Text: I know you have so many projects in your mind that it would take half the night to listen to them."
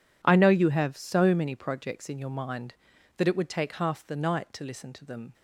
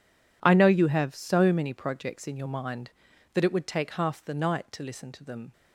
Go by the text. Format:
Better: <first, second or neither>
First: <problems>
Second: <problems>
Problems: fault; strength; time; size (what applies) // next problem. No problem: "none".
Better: neither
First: none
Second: none